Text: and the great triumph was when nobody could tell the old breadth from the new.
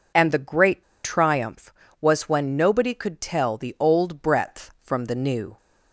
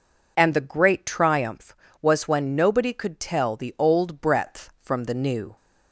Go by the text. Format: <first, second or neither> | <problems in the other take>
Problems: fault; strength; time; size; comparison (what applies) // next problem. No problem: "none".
second | pauses between "great" and "triumph"; slight; at 0.8 s; 0.21 s long